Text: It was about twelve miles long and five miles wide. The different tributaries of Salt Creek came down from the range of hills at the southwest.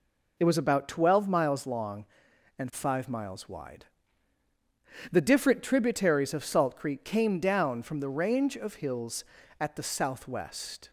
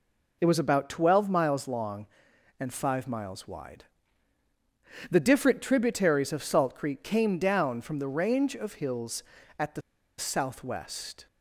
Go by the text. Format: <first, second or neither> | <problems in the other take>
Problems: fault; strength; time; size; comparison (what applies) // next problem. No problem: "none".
first | pauses between "the" and "southwest"; at 9.8 s; 0.37 s long